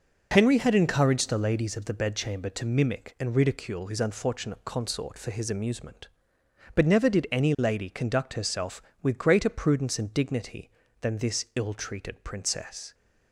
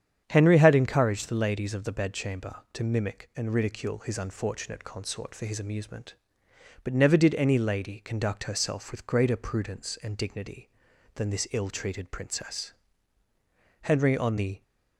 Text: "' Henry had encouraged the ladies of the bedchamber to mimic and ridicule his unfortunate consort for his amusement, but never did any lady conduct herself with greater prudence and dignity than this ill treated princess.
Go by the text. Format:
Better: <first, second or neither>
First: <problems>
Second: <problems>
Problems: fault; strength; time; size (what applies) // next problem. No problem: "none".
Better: first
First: none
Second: starts louder than the rest; strong; until 1.2 s; 9 dB // goes on to say "Henry on the"; noticeable; from 13.8 s on; 0.80 s long